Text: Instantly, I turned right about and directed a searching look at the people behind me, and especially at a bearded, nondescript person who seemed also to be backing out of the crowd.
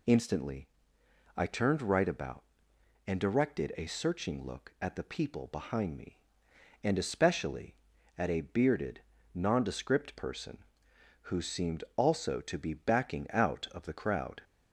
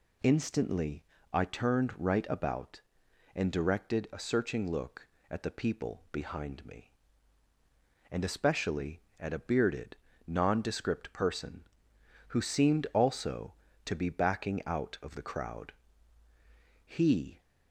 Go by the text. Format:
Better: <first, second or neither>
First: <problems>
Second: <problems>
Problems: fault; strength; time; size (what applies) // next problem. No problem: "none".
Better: first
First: none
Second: goes on to say "He"; from 16.8 s on; 0.56 s long